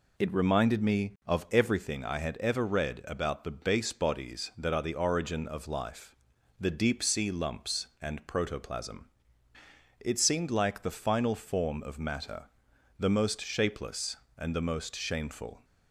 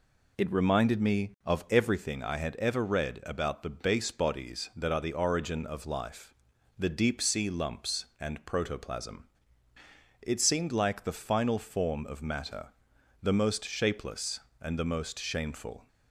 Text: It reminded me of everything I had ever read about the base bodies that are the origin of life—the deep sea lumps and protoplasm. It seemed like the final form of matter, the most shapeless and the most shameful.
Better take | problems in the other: neither | none

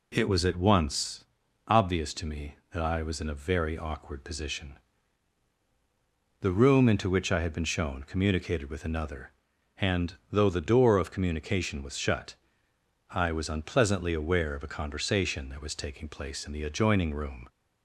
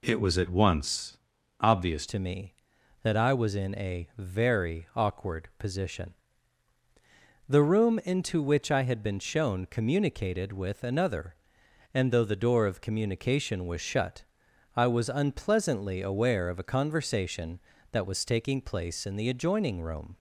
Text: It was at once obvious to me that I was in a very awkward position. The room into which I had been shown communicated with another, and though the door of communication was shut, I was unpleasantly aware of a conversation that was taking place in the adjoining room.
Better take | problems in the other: first | pauses between "once" and "obvious"; noticeable; at 1.1 s; 0.46 s long; noticeable in the first // changes voice at "to"; from 2.0 s on; 18.1 s long

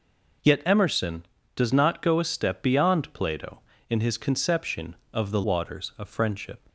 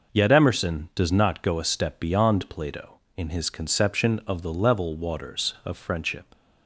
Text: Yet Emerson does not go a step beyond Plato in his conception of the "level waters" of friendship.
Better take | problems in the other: second | skips "level"; at 5.4 s

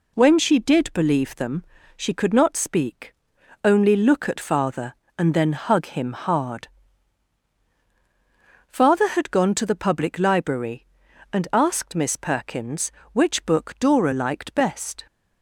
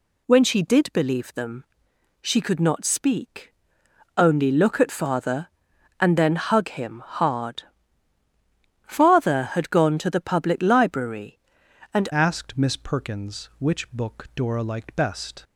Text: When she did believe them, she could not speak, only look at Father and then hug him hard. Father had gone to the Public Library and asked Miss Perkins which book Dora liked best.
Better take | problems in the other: first | changes voice at "asked"; from 12.1 s on; 3.3 s long

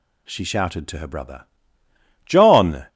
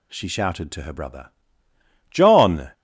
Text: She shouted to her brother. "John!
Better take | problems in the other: neither | none

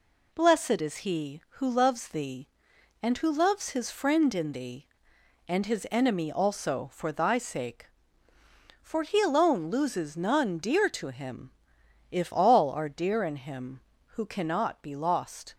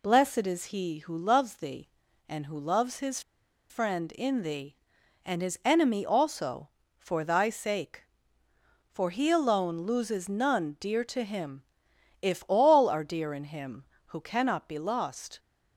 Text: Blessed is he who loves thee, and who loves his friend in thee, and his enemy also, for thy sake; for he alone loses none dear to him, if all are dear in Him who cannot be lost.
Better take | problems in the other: first | pauses between "his" and "friend"; noticeable; at 3.2 s; 0.49 s long

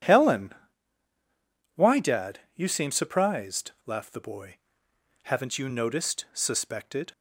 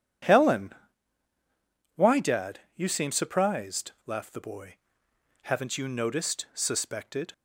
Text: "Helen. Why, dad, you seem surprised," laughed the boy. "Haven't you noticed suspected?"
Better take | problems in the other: neither | none

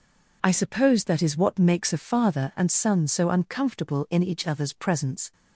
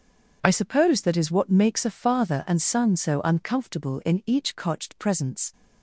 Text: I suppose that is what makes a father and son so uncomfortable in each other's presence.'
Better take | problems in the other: first | says "cotched" for "other's"; at 4.5 s

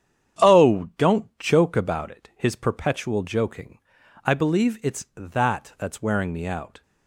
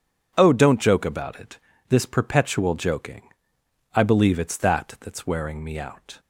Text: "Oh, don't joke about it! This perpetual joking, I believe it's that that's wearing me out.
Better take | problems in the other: second | starts louder than the rest; strong; until 1.6 s; 9 dB // says "His" for "This"; at 2.3 s

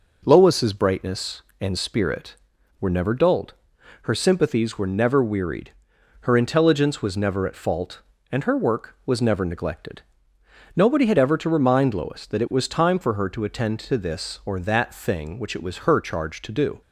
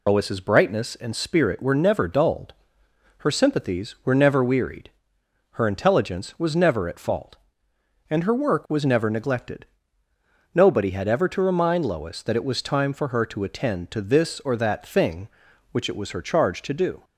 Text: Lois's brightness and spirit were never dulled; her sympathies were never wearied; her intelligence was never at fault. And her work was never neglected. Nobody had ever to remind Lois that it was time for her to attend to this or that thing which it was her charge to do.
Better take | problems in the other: first | loses the start of "Lois's"; at 0.0 s; 60 ms

